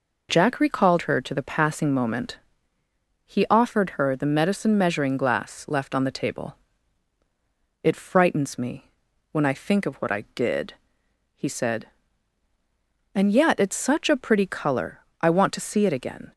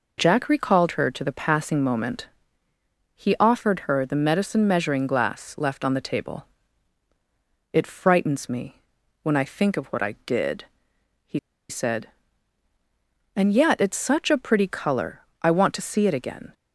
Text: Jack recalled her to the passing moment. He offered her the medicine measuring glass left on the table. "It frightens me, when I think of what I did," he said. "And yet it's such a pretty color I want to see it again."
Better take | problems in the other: first | pauses between "he" and "said"; slight; at 11.3 s; 0.30 s long // pauses between "color" and "I"; slight; at 15.2 s; 0.22 s long; slight in the first

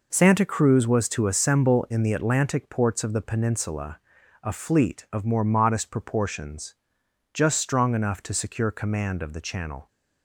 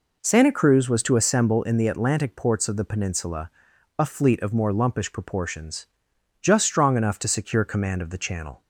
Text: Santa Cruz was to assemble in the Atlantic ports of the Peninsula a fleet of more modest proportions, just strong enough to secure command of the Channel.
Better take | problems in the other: first | pauses between "Peninsula" and "a"; noticeable; at 3.4 s; 0.48 s long; also in the first // says "lumpish" for "modest"; at 4.7 s

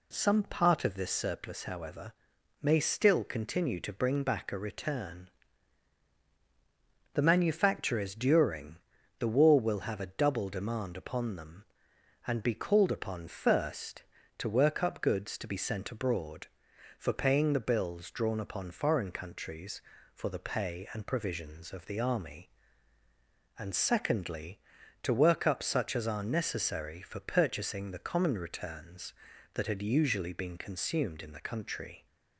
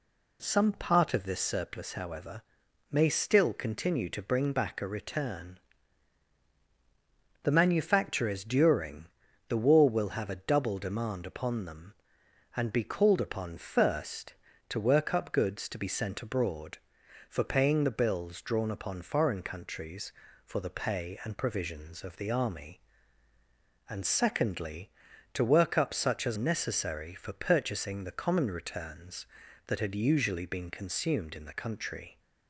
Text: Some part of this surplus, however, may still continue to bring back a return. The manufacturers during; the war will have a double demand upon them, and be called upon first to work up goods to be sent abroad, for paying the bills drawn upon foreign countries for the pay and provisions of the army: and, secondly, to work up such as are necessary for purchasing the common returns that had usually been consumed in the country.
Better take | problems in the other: first | skips "are"; at 26.3 s

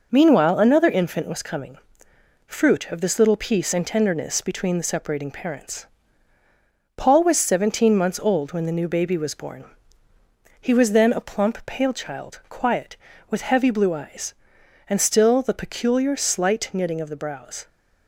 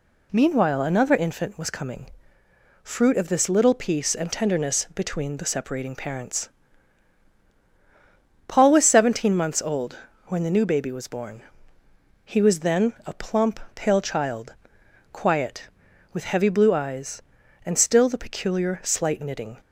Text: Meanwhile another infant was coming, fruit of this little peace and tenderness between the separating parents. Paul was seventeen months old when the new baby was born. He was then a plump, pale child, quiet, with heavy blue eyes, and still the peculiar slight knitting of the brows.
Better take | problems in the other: first | pauses between "old" and "when"; slight; at 9.9 s; 0.30 s long // stops before "of the brows"; at 19.6 s

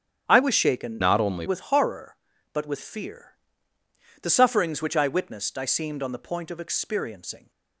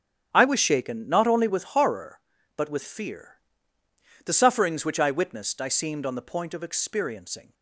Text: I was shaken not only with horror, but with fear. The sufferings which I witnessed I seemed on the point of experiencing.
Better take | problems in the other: second | starts louder than the rest; strong; until 1.2 s; 8.5 dB; strong in the second // changes voice from "not" to "only"; from 1.0 to 1.4 s; 0.4 s long

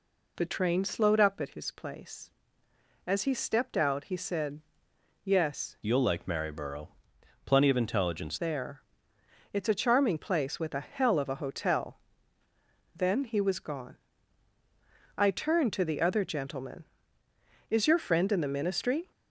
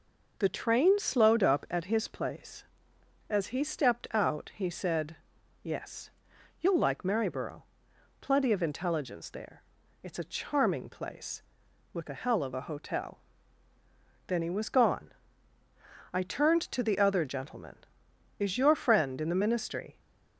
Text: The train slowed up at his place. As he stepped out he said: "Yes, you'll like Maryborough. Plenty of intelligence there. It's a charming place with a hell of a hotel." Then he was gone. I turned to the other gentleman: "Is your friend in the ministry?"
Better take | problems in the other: second | changes voice from "you'll" to "intelligence"; from 5.8 to 8.3 s; 2.5 s long

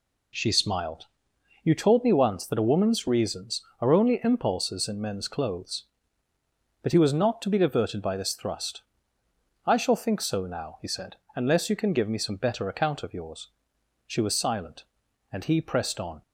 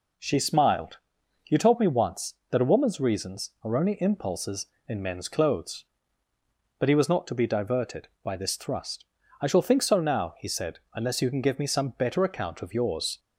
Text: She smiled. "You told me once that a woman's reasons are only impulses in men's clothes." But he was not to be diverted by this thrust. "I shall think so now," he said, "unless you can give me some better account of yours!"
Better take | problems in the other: second | goes on to say "She was silent and he pressed on"; strong; from 14.0 s on; 2.1 s long

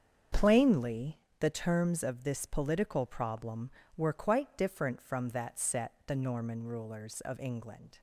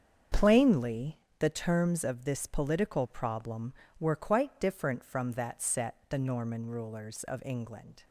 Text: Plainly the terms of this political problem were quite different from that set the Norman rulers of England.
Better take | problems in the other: neither | starts louder than the rest; strong; the same in both // pauses between "Plainly" and "the"; slight; the same in both // pauses between "set" and "the"; slight; the same in both

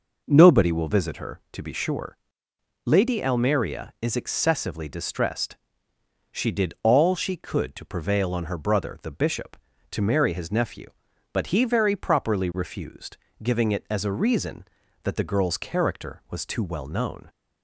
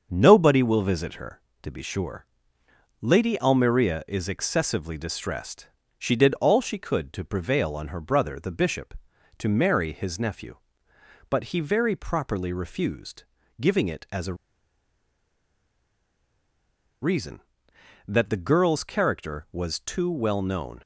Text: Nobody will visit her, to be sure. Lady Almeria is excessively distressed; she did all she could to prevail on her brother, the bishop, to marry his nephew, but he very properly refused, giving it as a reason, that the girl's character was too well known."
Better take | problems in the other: first | starts louder than the rest; until 1.1 s; 6.5 dB // pauses between "a" and "reason"; strong; at 14.3 s; 2.6 s long

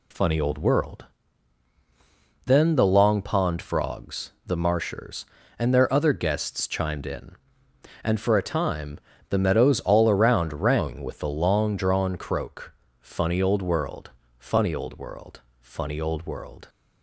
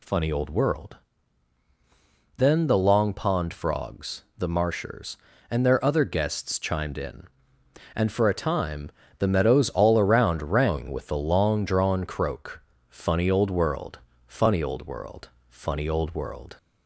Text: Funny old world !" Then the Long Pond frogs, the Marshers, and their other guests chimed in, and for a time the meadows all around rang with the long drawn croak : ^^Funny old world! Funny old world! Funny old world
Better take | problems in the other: first | gets louder; noticeable; throughout; 5.5 dB // pauses between "time" and "the"; slight; at 8.9 s; 0.28 s long; slight in the first

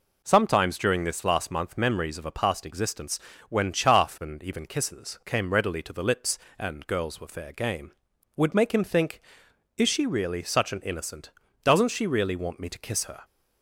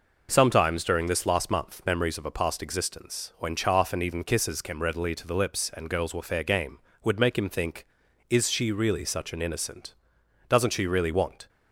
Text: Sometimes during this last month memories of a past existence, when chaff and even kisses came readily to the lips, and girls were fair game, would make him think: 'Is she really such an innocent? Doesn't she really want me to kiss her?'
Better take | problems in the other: first | stops before "me to kiss her"; at 11.4 s

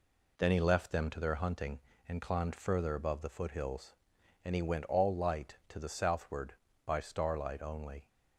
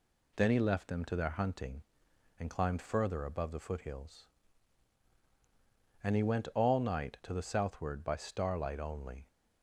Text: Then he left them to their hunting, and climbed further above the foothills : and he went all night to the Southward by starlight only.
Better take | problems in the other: second | says "light" for "night"; at 5.1 s

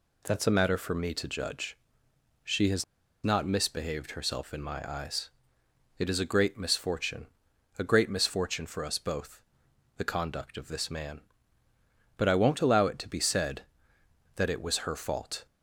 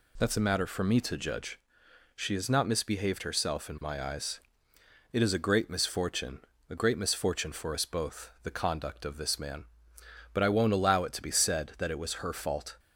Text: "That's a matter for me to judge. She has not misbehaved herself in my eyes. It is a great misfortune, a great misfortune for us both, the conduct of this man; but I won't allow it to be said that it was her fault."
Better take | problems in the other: second | pauses between "has" and "not"; at 2.8 s; 0.39 s long

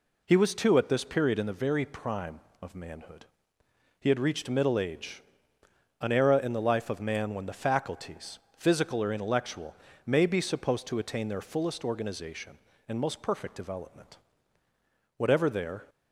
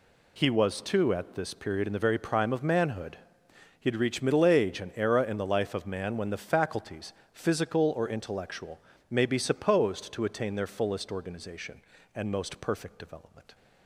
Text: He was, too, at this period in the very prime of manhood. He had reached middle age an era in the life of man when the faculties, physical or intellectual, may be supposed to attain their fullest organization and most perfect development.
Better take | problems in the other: second | pauses between "age" and "an"; noticeable; at 5.2 s; 0.80 s long // goes on to say "Whatever there"; noticeable; from 15.1 s on; 0.68 s long

